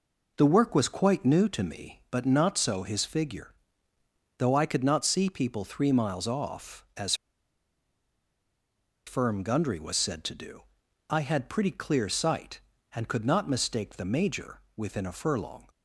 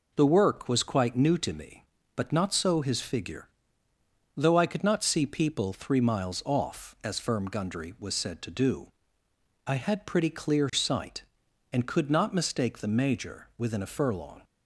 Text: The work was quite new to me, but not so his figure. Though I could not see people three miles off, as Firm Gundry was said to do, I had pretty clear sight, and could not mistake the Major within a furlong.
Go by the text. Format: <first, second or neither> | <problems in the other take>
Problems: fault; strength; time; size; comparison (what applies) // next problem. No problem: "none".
second | pauses between "as" and "Firm"; strong; at 7.1 s; 1.9 s long // pauses between "Major" and "within"; slight; at 14.6 s; 0.16 s long